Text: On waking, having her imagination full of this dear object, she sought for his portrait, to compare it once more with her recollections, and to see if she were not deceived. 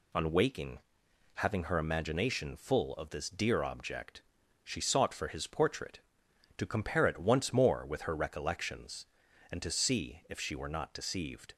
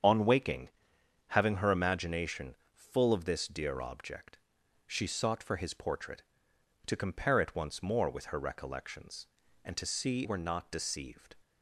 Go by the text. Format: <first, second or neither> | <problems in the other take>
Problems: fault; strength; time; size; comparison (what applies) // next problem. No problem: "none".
first | starts louder than the rest; strong; until 1.6 s; 7.5 dB // pauses between "imagination" and "full"; slight; at 2.5 s; 0.18 s long // skips "if she"; at 10.2 s